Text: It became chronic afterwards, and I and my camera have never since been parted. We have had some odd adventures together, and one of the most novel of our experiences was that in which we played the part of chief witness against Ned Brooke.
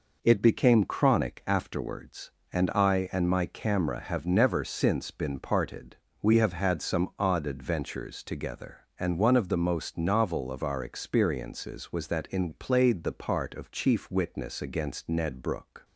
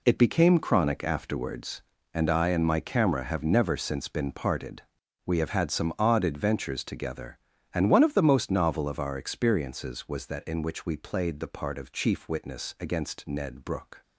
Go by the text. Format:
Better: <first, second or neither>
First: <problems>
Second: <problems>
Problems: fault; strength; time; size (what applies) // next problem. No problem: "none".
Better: second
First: skips "which we"; at 12.4 s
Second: none